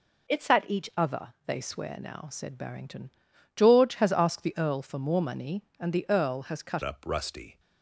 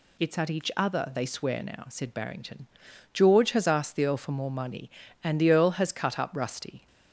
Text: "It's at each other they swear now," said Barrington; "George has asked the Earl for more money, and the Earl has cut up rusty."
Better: second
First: changes voice at "up"; from 6.8 s on; 0.7 s long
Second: none

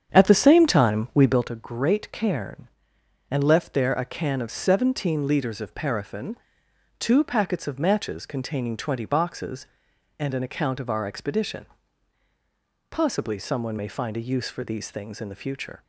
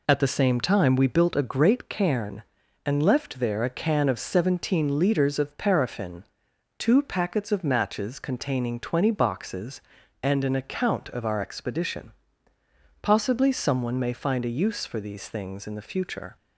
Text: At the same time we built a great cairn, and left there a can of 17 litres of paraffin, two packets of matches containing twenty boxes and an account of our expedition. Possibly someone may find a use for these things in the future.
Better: second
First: starts louder than the rest; strong; until 1.5 s; 8 dB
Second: none

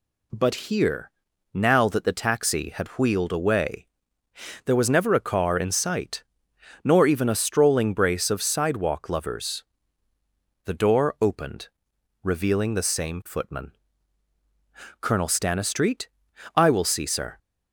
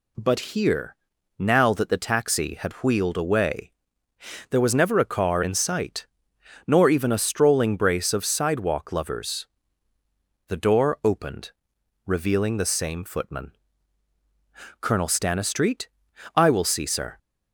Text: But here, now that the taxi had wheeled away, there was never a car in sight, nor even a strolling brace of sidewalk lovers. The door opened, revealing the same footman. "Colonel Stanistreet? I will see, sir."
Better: neither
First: none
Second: none

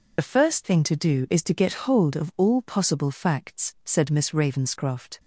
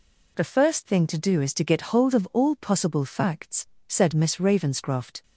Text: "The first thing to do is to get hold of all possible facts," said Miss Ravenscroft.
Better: second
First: loses the start of "The"; at 0.1 s; 50 ms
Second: none

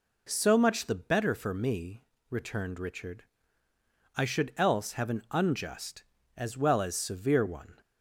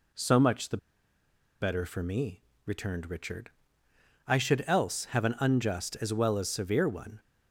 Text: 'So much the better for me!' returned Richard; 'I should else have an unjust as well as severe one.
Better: first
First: none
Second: pauses between "the" and "better"; noticeable; at 0.7 s; 0.83 s long

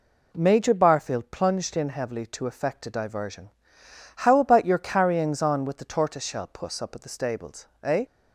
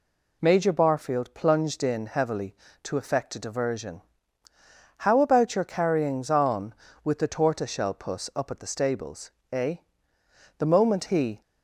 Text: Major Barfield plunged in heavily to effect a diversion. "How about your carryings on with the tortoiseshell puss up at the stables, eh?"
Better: first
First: none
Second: goes on to say "The moment he"; noticeable; from 10.5 s on; 0.82 s long

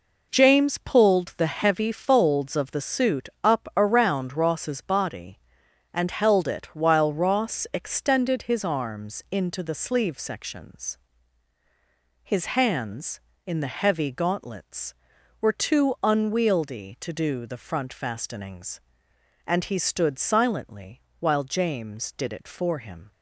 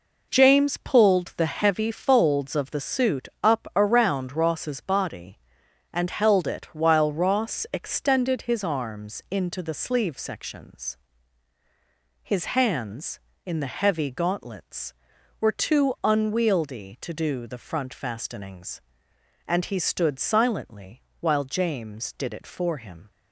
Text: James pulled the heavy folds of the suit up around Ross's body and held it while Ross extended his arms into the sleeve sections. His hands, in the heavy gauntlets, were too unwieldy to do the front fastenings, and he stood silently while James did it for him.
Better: neither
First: pauses between "silently" and "while"; slight; at 20.9 s; 0.18 s long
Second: pauses between "silently" and "while"; slight; at 21.0 s; 0.18 s long

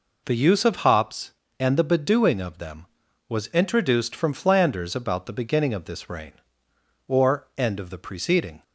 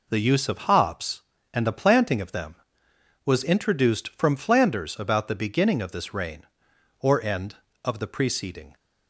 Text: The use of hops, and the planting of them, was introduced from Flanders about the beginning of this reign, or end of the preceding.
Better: second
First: says "bedewing" for "planting"; at 1.8 s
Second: none

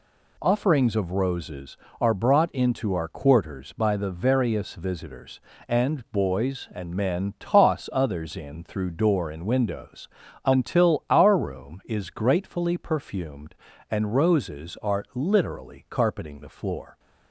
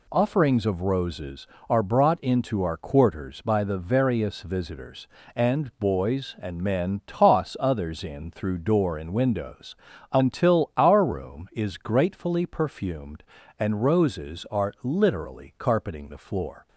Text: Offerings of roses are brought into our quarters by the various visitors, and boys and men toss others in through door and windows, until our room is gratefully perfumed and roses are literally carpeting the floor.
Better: neither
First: none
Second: none

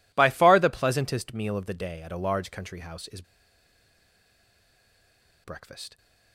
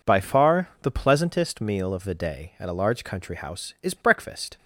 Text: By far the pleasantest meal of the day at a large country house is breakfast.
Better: second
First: pauses between "is" and "breakfast"; strong; at 3.2 s; 2.2 s long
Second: none

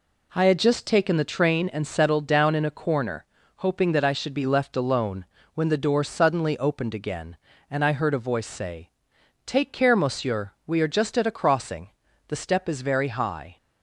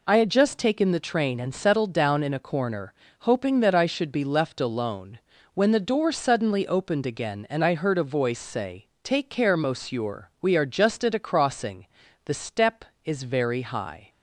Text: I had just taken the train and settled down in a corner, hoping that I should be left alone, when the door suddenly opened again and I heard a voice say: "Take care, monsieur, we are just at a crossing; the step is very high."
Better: neither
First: none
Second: none

